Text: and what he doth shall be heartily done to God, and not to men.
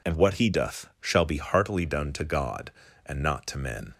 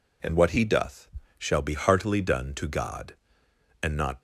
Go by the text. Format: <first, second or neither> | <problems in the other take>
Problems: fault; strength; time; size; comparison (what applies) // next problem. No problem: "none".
first | pauses between "doth" and "shall"; slight; at 1.0 s; 0.30 s long // stops before "to men"; at 4.1 s